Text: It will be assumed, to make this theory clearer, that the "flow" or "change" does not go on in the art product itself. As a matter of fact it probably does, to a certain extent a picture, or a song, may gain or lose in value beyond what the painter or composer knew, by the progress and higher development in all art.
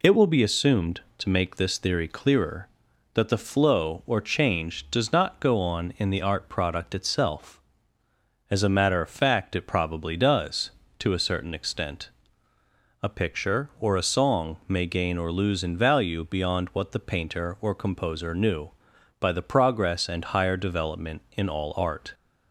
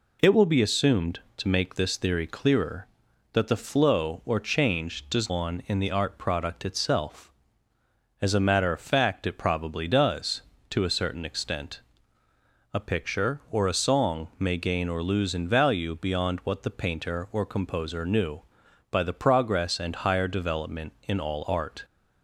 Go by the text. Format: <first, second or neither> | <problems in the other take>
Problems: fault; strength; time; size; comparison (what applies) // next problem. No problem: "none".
first | skips "not go"; at 5.2 s // pauses between "extent" and "a"; noticeable; at 11.8 s; 0.92 s long; noticeable in the first